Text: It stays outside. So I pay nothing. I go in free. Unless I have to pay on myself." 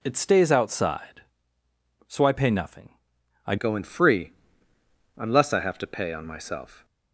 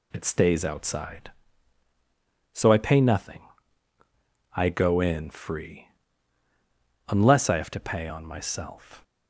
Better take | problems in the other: second | changes voice at "go"; from 3.5 s on; 3.3 s long

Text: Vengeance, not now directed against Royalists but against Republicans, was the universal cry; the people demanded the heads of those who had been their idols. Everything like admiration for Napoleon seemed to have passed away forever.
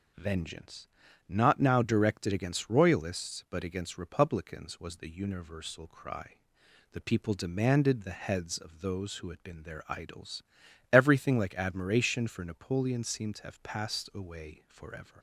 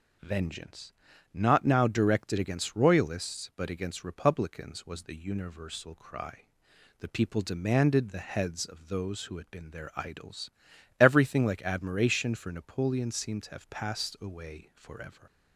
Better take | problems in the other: neither | none

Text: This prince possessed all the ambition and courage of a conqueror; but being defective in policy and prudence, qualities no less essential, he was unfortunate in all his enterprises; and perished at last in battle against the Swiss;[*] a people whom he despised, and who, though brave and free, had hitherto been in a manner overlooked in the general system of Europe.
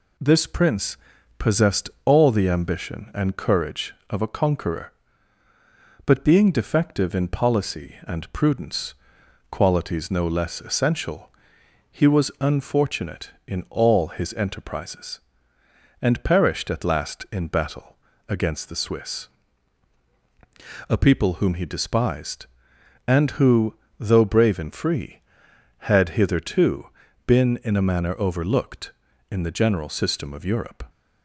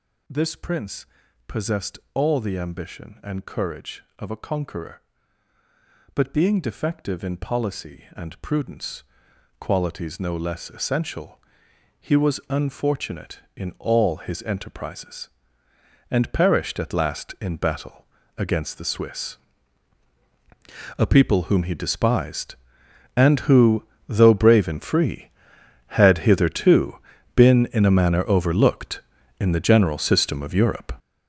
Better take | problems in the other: first | gets louder; strong; throughout; 8 dB // pauses between "prince" and "possessed"; at 1.0 s; 0.40 s long; also in the first // pauses between "battle" and "against"; slight; at 18.0 s; 0.32 s long; slight in the first // pauses between "hitherto" and "been"; at 26.9 s; 0.38 s long; also in the first

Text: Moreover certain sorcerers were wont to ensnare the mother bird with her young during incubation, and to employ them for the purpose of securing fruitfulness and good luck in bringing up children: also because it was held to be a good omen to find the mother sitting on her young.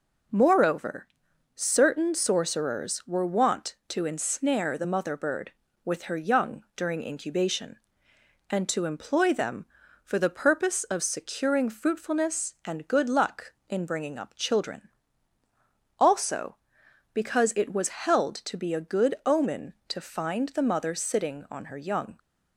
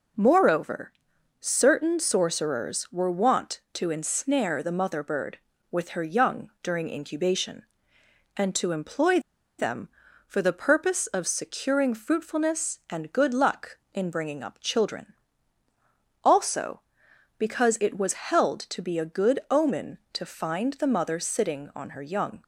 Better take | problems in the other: first | pauses between "Moreover" and "certain"; noticeable; at 0.9 s; 0.48 s long; noticeable in the first // pauses between "employ" and "them"; at 9.2 s; 0.38 s long

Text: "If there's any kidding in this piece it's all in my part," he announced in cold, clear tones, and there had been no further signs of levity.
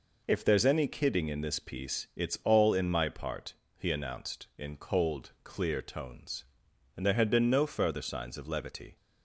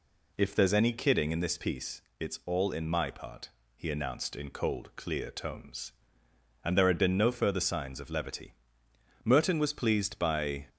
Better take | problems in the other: first | pauses between "piece" and "it's"; slight; at 2.0 s; 0.16 s long // goes on to say "Merton was pleased by"; from 9.2 s on; 1.4 s long

